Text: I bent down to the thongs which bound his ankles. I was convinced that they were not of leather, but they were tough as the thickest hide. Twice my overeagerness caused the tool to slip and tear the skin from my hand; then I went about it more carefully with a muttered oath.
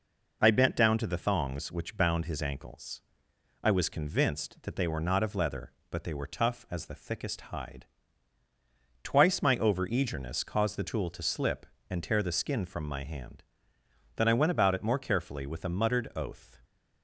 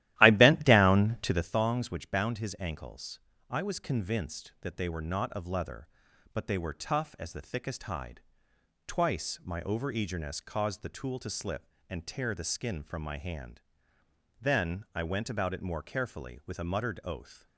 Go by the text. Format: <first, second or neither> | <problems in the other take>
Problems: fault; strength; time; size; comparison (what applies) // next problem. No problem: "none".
first | starts louder than the rest; strong; until 1.6 s; 14.5 dB